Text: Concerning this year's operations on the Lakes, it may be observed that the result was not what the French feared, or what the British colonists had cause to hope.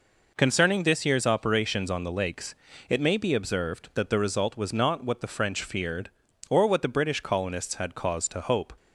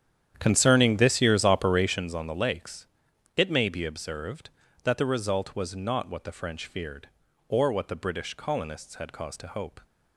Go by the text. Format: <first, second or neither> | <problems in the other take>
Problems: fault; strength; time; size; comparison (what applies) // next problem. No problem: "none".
first | starts louder than the rest; strong; until 2.1 s; 9.5 dB